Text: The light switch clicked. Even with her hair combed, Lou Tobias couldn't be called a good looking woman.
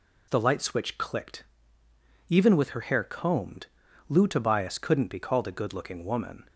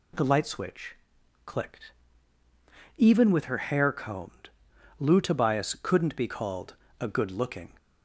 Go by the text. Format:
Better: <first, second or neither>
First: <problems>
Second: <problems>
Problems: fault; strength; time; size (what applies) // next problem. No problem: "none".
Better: first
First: none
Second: pauses between "switch" and "clicked"; noticeable; at 0.9 s; 0.50 s long // pauses between "called" and "a"; slight; at 6.7 s; 0.26 s long // stops before "woman"; at 7.7 s